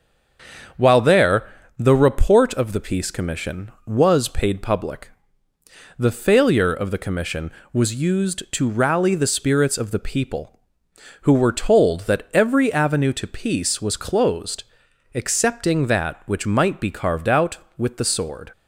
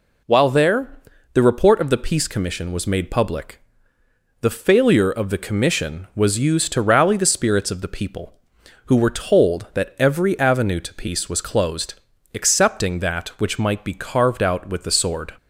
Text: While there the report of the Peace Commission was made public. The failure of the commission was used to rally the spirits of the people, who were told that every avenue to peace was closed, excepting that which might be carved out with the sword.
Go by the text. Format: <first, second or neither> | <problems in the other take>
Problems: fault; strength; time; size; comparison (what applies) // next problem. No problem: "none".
second | starts louder than the rest; until 2.0 s; 7 dB // pauses between "there" and "the"; slight; at 1.4 s; 0.28 s long; slight in the second // says "paid" for "made"; at 4.2 s